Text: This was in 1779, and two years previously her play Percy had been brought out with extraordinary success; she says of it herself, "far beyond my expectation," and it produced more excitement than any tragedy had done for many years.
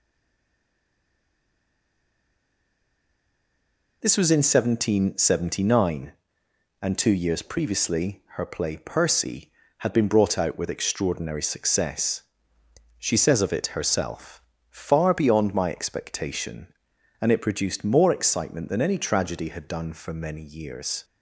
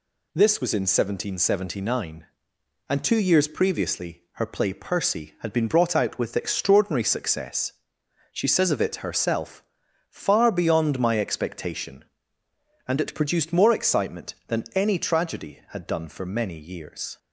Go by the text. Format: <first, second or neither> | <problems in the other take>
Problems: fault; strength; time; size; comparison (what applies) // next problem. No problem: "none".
second | stays silent before the first word; strong; until 4.0 s; 4.0 s long